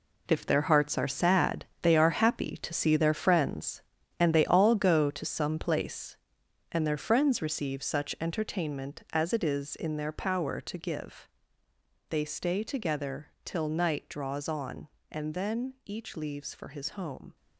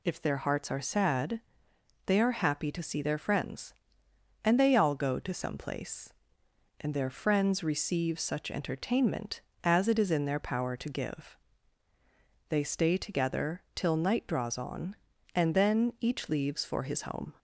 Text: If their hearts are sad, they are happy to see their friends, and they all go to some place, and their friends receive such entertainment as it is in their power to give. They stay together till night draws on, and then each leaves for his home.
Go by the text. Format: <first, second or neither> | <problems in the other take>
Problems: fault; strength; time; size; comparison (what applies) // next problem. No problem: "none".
second | gets quieter; strong; throughout; 10.5 dB // pauses between "together" and "till"; slight; at 13.2 s; 0.16 s long